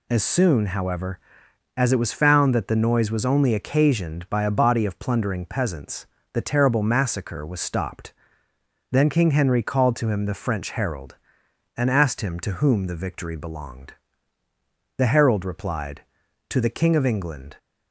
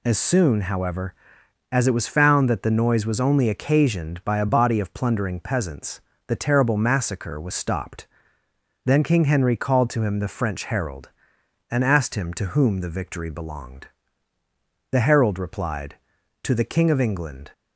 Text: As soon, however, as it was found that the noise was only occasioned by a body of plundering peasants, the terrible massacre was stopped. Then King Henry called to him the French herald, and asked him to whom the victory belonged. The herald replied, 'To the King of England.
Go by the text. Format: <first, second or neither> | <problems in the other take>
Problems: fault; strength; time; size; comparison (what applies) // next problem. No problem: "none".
neither | none